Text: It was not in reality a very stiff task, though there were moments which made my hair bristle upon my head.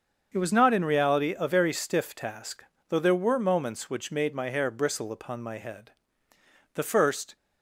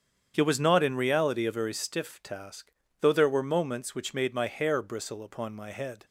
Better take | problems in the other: second | starts louder than the rest; until 1.3 s; 7 dB; strong in the second // goes on to say "The first"; noticeable; from 6.7 s on; 0.62 s long

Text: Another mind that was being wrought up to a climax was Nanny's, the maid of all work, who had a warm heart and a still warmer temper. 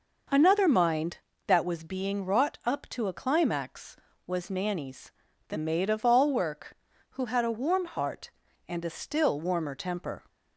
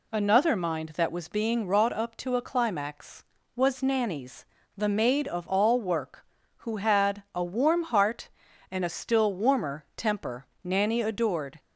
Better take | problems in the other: first | goes on to say "Nanny adored"; noticeable; from 10.6 s on; 0.96 s long

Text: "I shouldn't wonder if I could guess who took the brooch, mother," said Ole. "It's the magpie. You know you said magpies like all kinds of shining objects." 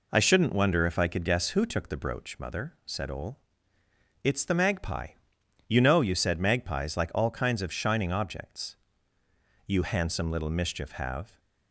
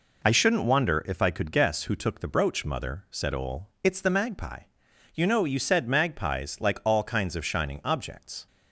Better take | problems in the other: second | goes on to say "You handsome little mischief have"; strong; from 9.6 s on; 1.7 s long

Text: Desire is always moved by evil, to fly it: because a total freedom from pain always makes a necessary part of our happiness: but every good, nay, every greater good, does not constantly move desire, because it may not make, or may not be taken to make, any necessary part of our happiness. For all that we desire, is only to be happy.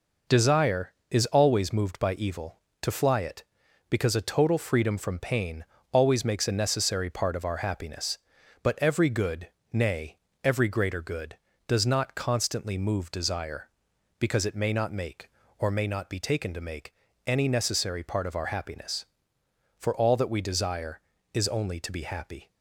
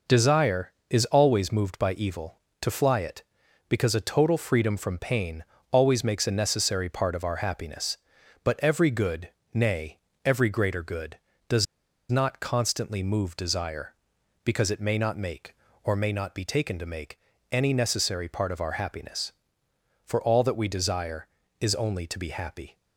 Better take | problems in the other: first | pauses between "pain" and "always"; slight; at 5.4 s; 0.30 s long; slight in the first // pauses between "does" and "not"; at 11.6 s; 0.44 s long

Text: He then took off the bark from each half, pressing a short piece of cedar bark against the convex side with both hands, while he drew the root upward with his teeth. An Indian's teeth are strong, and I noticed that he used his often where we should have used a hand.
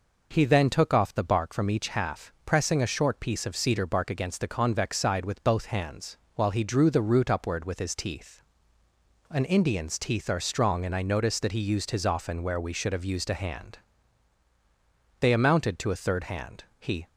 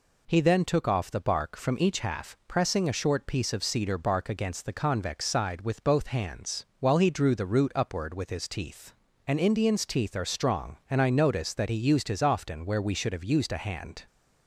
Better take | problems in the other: second | goes on to say "They amounted to a third hand He"; strong; from 15.1 s on; 1.8 s long

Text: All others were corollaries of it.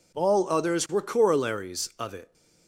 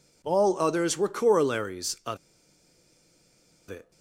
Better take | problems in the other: first | pauses between "of" and "it"; strong; at 2.1 s; 1.5 s long

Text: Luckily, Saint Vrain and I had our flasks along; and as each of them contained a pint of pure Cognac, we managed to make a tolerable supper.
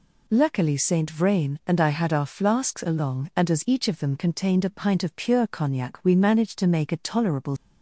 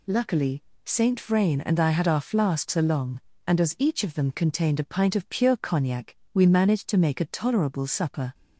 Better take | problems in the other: second | stops before "supper"; at 7.5 s

